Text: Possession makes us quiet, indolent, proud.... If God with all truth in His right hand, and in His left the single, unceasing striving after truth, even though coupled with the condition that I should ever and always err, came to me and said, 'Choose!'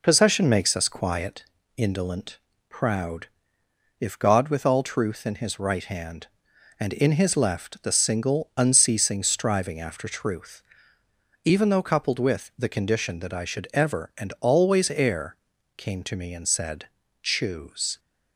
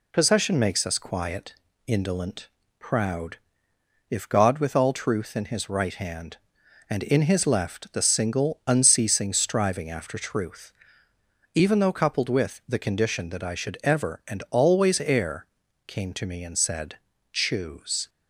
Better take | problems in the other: second | starts louder than the rest; noticeable; until 1.3 s; 4.5 dB

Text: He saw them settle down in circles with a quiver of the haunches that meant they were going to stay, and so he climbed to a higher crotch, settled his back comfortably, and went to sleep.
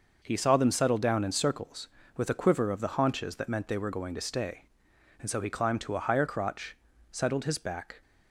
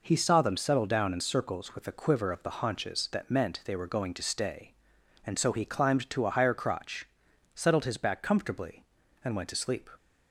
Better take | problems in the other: second | stops before "comfortably and went to sleep"; at 8.0 s

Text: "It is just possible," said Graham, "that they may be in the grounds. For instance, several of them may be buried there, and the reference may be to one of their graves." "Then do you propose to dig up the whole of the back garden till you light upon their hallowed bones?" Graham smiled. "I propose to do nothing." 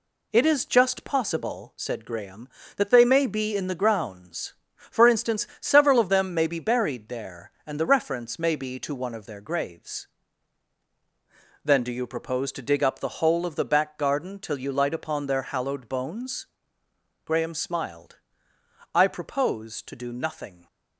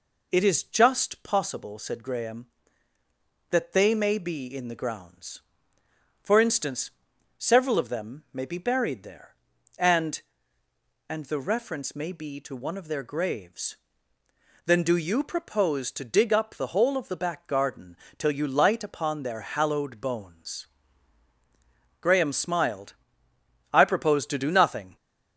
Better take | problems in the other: first | says "and" twice; at 11.0 s // pauses between "garden" and "till"; slight; at 17.9 s; 0.24 s long

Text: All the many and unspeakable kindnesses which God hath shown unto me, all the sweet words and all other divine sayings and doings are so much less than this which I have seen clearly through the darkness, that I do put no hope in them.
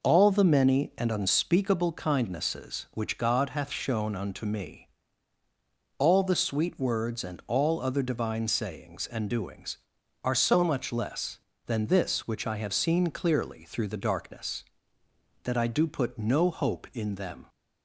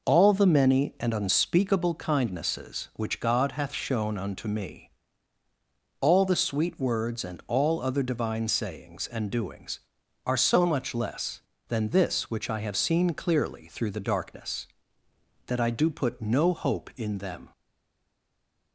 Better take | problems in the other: first | stays silent after the last word; noticeable; from 17.5 s on; 1.2 s long

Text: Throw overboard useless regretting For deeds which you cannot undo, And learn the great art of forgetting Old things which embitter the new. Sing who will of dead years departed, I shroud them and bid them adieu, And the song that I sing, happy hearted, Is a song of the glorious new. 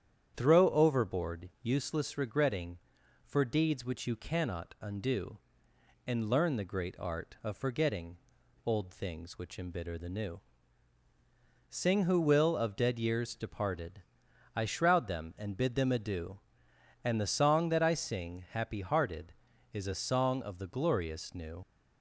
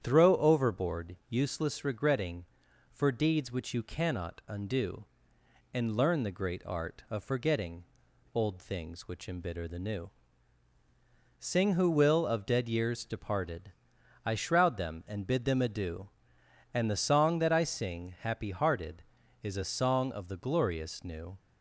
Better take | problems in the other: second | starts louder than the rest; strong; until 1.3 s; 9 dB; strong in the second // pauses between "forgetting" and "Old"; noticeable; at 8.1 s; 0.48 s long; noticeable in the second // leaves "new" unfinished; at 21.6 s; 50 ms

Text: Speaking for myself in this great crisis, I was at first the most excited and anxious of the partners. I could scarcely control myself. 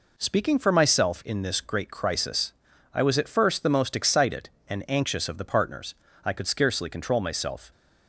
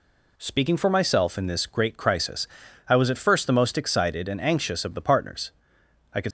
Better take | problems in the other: first | stops before "scarcely control myself"; at 6.2 s

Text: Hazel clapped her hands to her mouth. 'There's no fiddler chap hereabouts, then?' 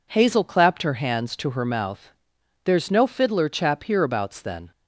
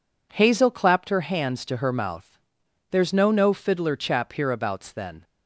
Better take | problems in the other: first | says "no" twice; at 3.3 s

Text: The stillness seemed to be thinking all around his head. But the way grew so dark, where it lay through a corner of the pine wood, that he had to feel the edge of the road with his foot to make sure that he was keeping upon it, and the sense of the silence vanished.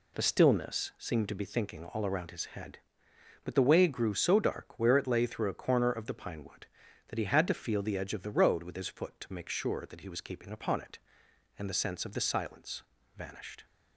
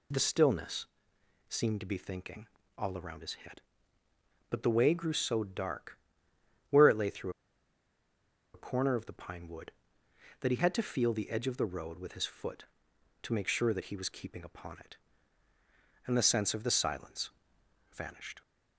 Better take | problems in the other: first | pauses between "stillness" and "seemed"; noticeable; at 0.8 s; 0.60 s long // pauses between "thinking" and "all"; slight; at 2.4 s; 0.32 s long // pauses between "through" and "a"; strong; at 7.2 s; 1.2 s long // pauses between "silence" and "vanished"; noticeable; at 17.3 s; 0.60 s long; slight in the first

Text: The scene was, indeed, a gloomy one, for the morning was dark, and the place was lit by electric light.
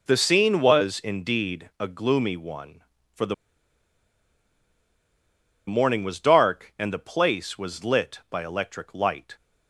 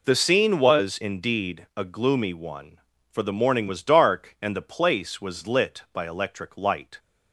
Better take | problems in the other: second | pauses between "the" and "morning"; strong; at 3.3 s; 2.3 s long

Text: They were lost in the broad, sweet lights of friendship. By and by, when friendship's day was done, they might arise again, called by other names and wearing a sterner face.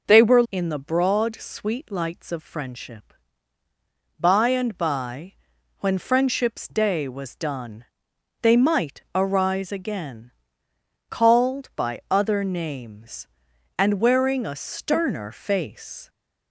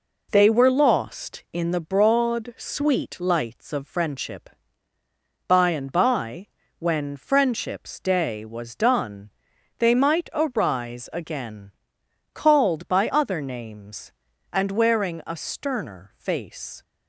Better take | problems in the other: second | skips "lost"; at 0.4 s

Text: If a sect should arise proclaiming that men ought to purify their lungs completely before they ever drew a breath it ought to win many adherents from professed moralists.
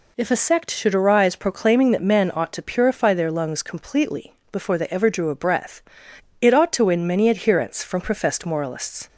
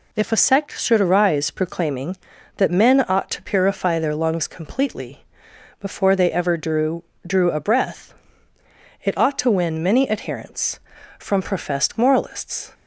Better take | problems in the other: first | pauses between "completely" and "before"; noticeable; at 5.2 s; 0.56 s long; slight in the first // says "drew" twice; at 7.2 s // pauses between "breath" and "it"; noticeable; at 8.1 s; 0.90 s long; noticeable in the first

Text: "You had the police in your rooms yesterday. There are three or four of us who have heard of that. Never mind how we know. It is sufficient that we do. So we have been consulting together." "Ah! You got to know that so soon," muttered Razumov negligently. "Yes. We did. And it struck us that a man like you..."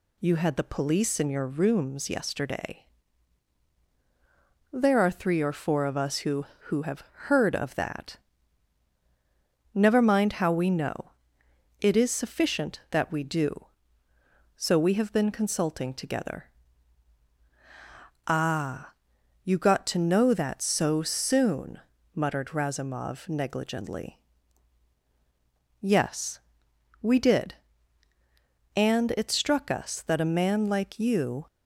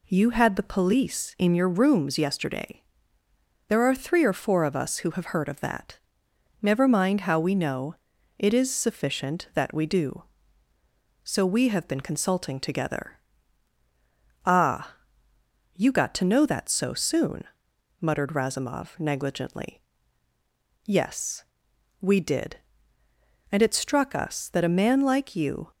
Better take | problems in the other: second | says "who" twice; at 6.6 s

